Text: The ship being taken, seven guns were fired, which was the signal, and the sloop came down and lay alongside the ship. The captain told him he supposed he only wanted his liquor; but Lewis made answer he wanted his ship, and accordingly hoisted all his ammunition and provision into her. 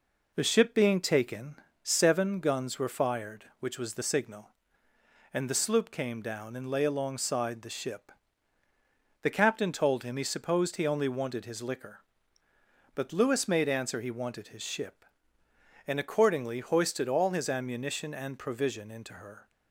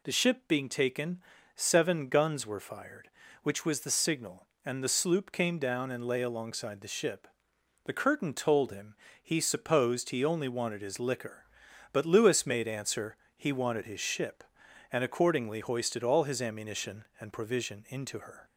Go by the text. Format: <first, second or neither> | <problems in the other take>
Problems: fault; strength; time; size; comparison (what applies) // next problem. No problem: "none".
first | says "curtain" for "captain"; at 7.9 s // pauses between "him" and "he"; slight; at 8.9 s; 0.26 s long // pauses between "answer" and "he"; slight; at 13.1 s; 0.20 s long